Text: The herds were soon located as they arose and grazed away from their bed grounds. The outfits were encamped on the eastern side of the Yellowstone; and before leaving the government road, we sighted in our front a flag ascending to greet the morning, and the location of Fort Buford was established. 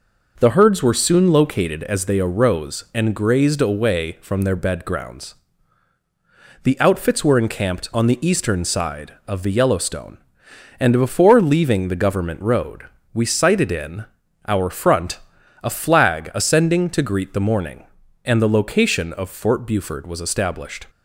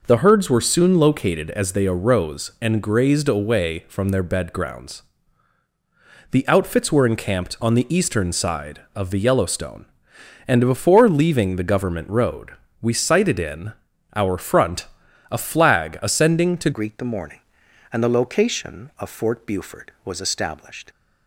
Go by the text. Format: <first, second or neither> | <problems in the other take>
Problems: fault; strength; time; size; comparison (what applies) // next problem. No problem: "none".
first | pauses between "in" and "our"; at 13.7 s; 0.42 s long; also in the first // pauses between "front" and "a"; at 14.8 s; 0.44 s long; also in the first // changes voice at "greet"; from 16.7 s on; 4.1 s long